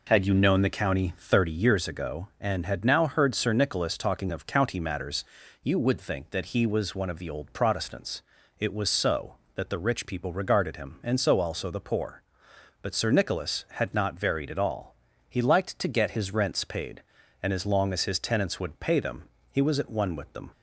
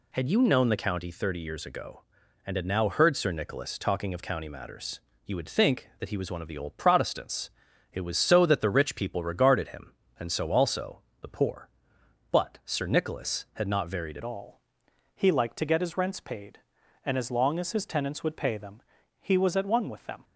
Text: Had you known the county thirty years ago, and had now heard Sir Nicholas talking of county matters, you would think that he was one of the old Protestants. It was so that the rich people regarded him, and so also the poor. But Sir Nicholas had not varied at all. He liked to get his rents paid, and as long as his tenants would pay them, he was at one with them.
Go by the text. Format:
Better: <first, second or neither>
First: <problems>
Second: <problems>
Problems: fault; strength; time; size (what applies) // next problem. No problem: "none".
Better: first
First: none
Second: pauses between "also" and "the"; slight; at 11.0 s; 0.22 s long // changes voice at "all"; from 14.2 s on; 6.0 s long